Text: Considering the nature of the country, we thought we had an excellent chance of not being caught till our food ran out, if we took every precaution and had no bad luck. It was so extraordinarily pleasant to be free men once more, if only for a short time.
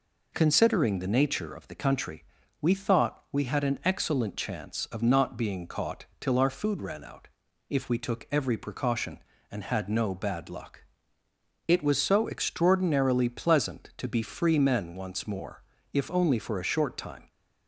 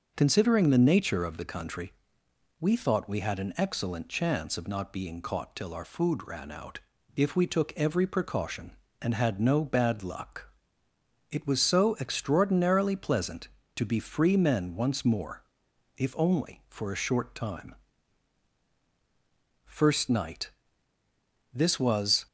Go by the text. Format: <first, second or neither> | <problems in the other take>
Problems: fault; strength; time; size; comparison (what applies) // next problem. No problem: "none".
first | goes on to say "First Night This was"; strong; from 17.7 s on; 4.5 s long